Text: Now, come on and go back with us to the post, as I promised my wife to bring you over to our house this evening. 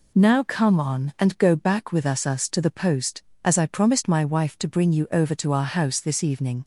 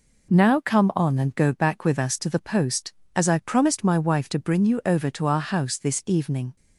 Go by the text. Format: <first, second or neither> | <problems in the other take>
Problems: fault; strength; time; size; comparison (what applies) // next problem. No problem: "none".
second | says "us" twice; at 2.2 s